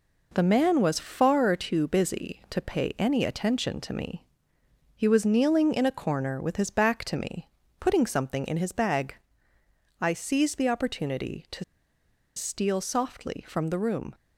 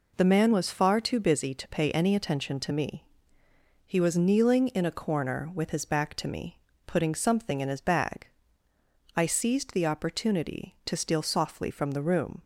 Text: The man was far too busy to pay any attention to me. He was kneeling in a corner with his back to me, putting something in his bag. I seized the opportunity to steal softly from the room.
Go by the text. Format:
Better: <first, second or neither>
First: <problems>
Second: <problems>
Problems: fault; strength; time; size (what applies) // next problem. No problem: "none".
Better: second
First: pauses between "to" and "steal"; noticeable; at 11.6 s; 0.72 s long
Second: none